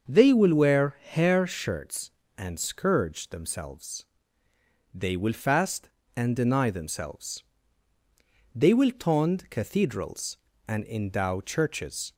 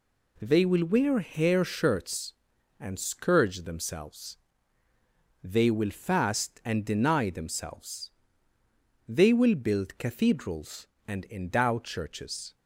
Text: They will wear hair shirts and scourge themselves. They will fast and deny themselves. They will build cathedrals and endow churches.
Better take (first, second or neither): second